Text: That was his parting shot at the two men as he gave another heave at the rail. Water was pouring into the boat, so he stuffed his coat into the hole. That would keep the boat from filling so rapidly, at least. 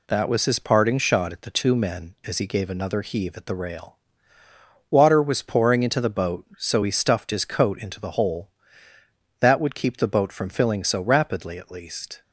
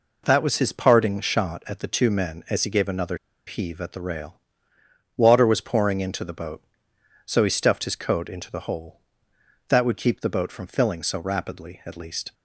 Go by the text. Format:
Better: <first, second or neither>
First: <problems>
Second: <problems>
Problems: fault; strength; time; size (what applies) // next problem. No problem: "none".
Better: first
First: none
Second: pauses between "another" and "heave"; slight; at 3.1 s; 0.30 s long